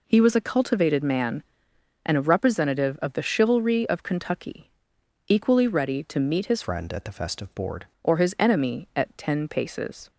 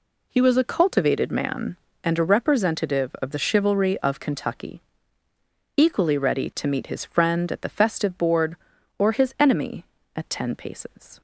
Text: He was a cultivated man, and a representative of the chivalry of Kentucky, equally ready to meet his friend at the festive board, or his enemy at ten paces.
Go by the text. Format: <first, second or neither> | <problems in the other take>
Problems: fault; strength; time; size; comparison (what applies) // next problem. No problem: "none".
second | changes voice from "friend" to "board"; from 6.6 to 7.8 s; 1.2 s long